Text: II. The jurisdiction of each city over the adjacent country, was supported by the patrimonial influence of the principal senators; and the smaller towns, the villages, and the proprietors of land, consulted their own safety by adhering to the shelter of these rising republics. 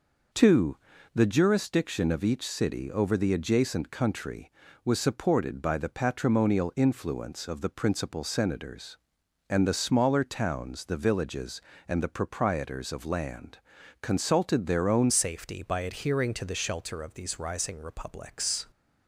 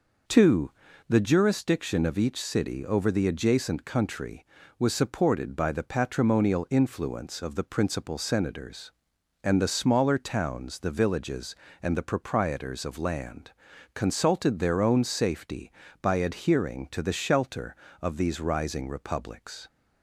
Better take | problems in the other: second | changes voice at "safety"; from 15.0 s on; 3.6 s long

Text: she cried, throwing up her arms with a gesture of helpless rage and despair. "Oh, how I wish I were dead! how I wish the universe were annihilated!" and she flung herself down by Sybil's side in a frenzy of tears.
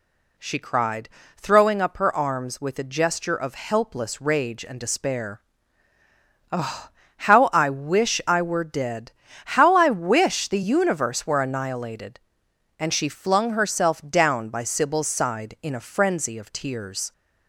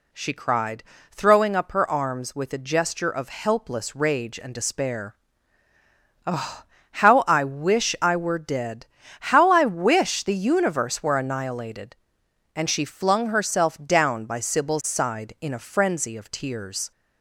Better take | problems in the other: neither | none

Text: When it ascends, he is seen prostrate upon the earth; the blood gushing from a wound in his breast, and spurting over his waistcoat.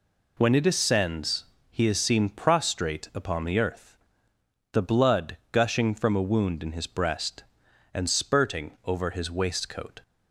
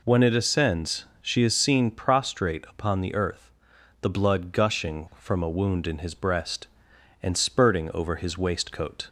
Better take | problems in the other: first | says "she" for "he"; at 1.2 s

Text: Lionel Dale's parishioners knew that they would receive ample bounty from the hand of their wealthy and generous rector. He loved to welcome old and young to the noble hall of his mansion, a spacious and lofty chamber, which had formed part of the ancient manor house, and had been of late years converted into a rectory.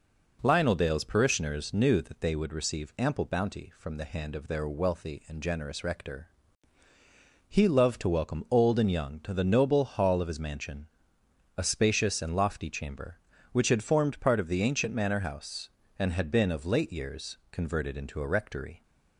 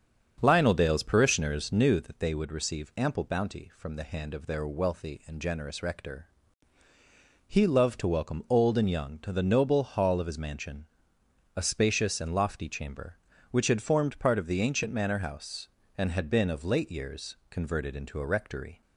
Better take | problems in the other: first | starts louder than the rest; strong; until 1.9 s; 7.5 dB // pauses between "years" and "converted"; slight; at 17.3 s; 0.16 s long; slight in the first

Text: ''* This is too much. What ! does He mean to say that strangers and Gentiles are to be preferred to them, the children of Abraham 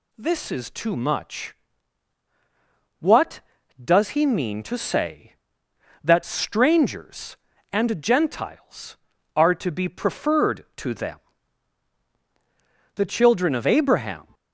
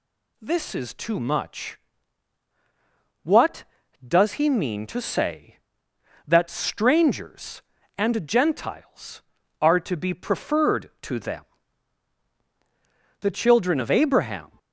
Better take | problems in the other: neither | none

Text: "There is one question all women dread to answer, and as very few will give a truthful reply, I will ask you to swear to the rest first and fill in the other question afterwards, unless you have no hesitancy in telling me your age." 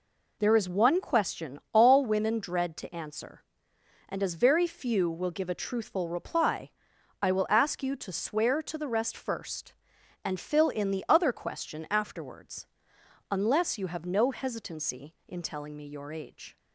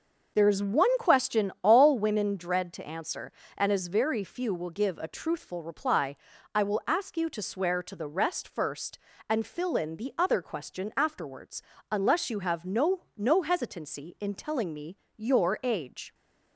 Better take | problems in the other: first | starts louder than the rest; noticeable; until 1.3 s; 6 dB // says "no" twice; at 13.1 s // pauses between "me" and "your"; slight; at 14.9 s; 0.20 s long

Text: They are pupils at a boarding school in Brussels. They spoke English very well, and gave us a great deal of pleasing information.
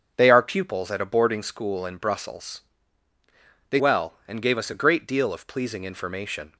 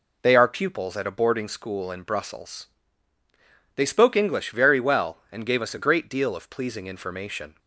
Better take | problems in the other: second | starts louder than the rest; until 1.1 s; 6.5 dB // skips "spoke English very"; at 3.7 s

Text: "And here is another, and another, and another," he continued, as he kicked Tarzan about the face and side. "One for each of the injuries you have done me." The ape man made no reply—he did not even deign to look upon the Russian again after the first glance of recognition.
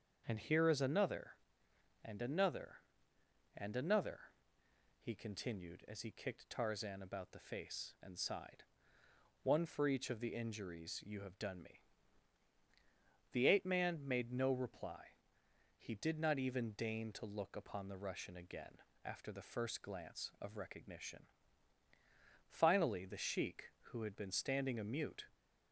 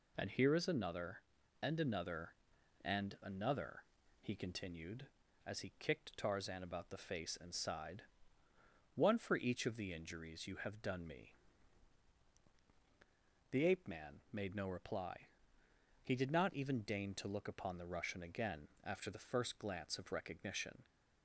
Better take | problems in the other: second | starts louder than the rest; until 1.2 s; 6.5 dB // pauses between "again" and "after"; slight; at 18.8 s; 0.24 s long; slight in the second // goes on to say "Finally the sheik who had been standing a mute"; strong; from 22.4 s on; 2.8 s long

